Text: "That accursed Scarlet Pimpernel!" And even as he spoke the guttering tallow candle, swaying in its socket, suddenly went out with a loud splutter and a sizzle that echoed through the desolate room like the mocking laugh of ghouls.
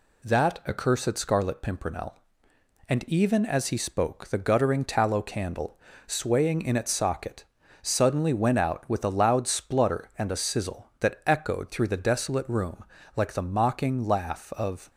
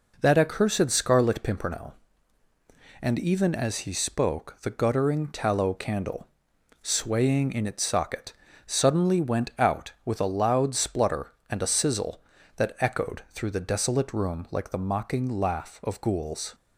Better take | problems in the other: second | pauses between "room" and "like"; slight; at 12.8 s; 0.32 s long // stops before "ghouls"; at 14.8 s

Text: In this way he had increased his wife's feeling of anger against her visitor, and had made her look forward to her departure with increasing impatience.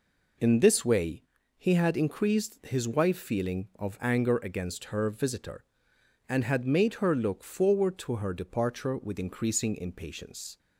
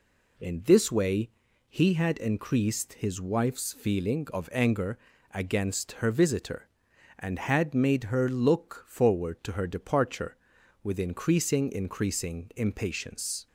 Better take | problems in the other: first | pauses between "way" and "he"; at 1.3 s; 0.38 s long; slight in the first // pauses between "anger" and "against"; slight; at 4.9 s; 0.36 s long // says "increasing" twice; at 11.7 s

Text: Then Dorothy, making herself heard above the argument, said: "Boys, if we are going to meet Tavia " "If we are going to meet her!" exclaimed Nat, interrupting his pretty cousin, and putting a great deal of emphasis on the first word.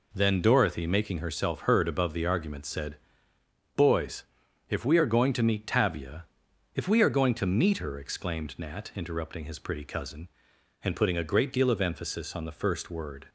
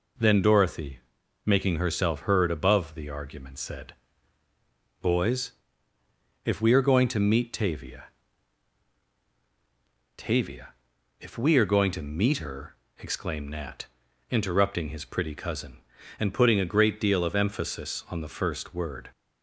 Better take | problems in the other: first | says "Tavia" twice; at 10.1 s

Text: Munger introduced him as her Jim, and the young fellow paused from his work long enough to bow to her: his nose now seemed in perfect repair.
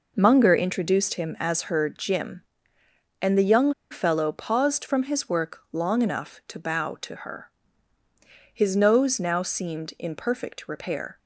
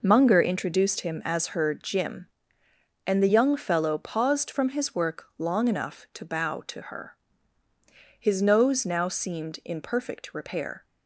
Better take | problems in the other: second | pauses between "young" and "fellow"; slight; at 3.7 s; 0.17 s long

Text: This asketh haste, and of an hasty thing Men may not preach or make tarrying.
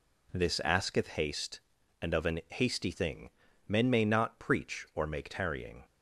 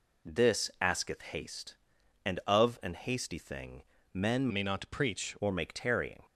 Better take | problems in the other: first | pauses between "thing" and "Men"; slight; at 3.8 s; 0.30 s long; slight in the first // changes voice from "may" to "preach"; from 4.5 to 5.3 s; 0.8 s long

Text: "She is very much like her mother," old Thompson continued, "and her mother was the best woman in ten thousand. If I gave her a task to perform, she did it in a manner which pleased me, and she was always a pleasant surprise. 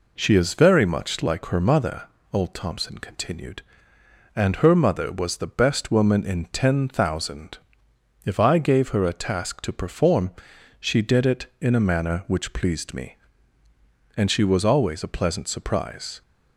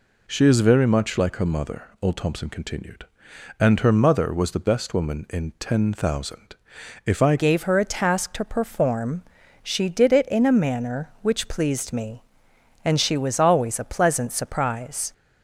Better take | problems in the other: first | changes voice at "gave"; from 7.3 s on; 7.8 s long

